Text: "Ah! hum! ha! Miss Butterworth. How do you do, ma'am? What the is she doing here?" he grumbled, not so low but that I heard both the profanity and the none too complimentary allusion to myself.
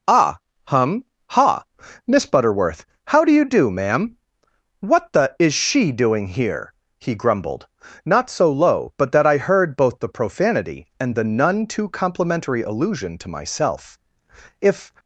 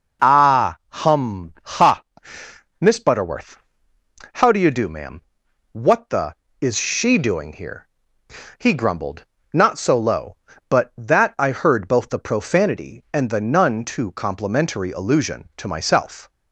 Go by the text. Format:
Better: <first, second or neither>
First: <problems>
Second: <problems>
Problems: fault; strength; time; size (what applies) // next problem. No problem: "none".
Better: second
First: goes on to say "If"; slight; from 14.5 s on; 0.32 s long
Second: none